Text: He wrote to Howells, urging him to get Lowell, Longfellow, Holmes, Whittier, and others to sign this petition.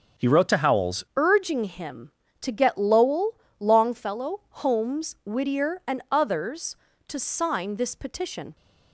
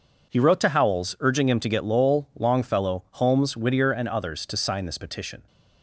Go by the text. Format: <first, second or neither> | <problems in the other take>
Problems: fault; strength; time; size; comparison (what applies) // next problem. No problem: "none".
second | starts louder than the rest; until 1.3 s; 6.5 dB // changes voice at "urging"; from 1.1 s on; 7.4 s long